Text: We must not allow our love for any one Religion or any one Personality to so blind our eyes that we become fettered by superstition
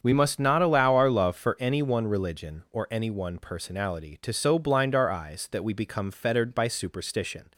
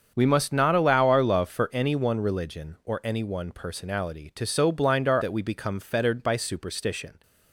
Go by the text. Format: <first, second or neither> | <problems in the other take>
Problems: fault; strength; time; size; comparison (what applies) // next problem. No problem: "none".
first | starts louder than the rest; strong; until 1.1 s; 7 dB; strong in the first // skips "eyes"; at 5.2 s